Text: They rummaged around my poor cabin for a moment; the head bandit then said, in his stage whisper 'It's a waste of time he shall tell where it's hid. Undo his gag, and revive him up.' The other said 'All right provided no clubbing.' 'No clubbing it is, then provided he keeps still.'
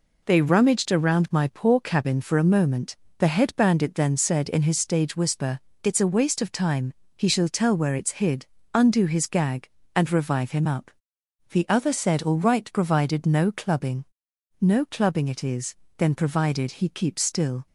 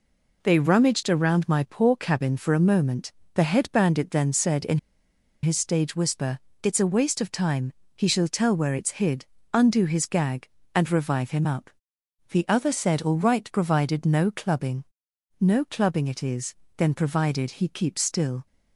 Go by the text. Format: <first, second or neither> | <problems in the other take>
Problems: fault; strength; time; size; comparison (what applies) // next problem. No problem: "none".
first | pauses between "in" and "his"; noticeable; at 4.7 s; 0.65 s long // pauses between "whisper" and "It's"; slight; at 6.3 s; 0.24 s long; slight in the first // pauses between "time" and "he"; slight; at 7.7 s; 0.20 s long; slight in the first